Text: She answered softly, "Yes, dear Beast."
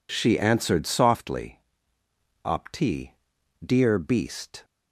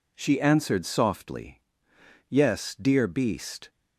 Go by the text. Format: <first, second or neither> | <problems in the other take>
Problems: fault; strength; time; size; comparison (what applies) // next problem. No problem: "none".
second | says "Opti" for "Yes"; at 2.4 s